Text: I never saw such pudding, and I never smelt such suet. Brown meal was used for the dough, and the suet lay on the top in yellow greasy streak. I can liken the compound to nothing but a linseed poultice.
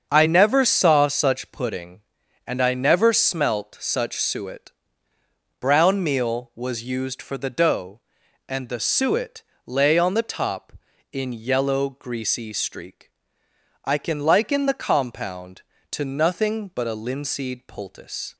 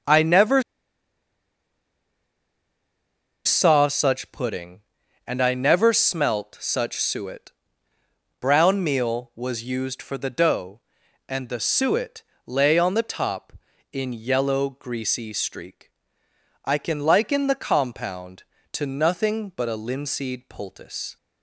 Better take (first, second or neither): first